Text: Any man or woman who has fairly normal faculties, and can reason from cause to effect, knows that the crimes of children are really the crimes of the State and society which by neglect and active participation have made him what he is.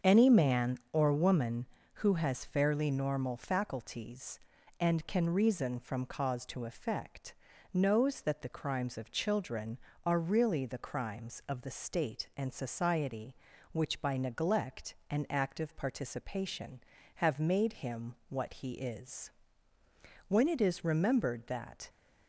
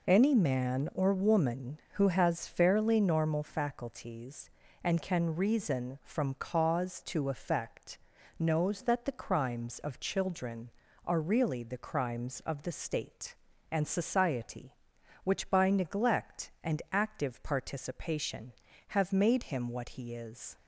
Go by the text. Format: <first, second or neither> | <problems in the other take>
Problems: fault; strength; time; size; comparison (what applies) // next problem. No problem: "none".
second | starts louder than the rest; until 1.1 s; 7 dB // pauses between "him" and "what"; slight; at 18.1 s; 0.16 s long // goes on to say "When it is remembered that"; from 20.2 s on; 1.6 s long